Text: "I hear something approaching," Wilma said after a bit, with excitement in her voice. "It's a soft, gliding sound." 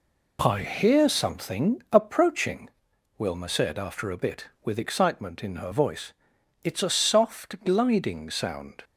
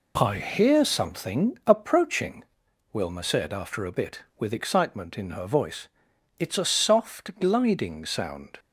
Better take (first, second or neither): neither